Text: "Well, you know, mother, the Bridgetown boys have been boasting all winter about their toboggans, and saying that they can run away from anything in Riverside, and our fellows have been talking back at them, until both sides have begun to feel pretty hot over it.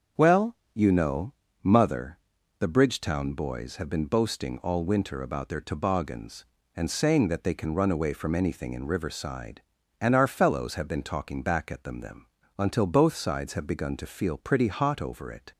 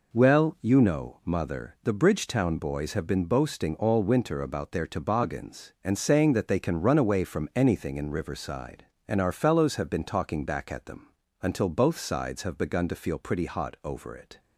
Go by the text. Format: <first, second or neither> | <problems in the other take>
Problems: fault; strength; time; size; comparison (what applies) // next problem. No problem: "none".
second | starts louder than the rest; until 1.6 s; 6.5 dB // says "them" twice; at 11.9 s